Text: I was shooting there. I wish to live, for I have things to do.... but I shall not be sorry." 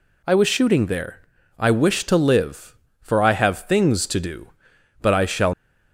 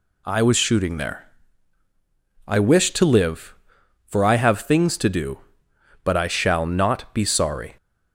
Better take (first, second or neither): second